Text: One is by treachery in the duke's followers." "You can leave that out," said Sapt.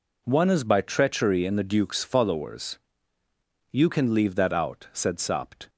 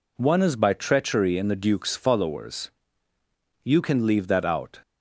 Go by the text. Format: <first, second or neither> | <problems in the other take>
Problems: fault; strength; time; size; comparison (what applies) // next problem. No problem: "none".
first | stops before "said Sapt"; at 4.8 s